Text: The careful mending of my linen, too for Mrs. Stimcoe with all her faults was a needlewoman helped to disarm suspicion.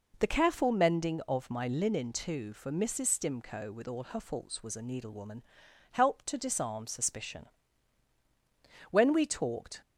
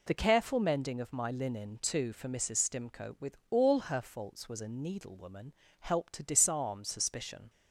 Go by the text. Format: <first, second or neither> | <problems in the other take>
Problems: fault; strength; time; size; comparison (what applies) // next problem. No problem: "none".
second | pauses between "needlewoman" and "helped"; noticeable; at 5.4 s; 0.48 s long; slight in the second // goes on to say "When we talked"; noticeable; from 8.9 s on; 0.90 s long